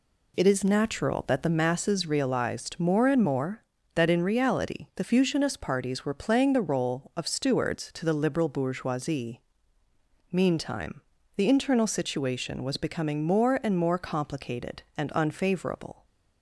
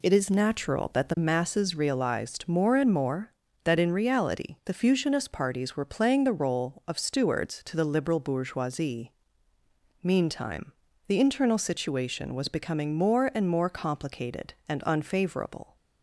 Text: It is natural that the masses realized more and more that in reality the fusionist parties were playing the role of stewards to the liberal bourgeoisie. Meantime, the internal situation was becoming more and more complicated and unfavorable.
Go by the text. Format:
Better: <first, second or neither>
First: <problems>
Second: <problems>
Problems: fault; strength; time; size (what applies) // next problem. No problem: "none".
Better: neither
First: none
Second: none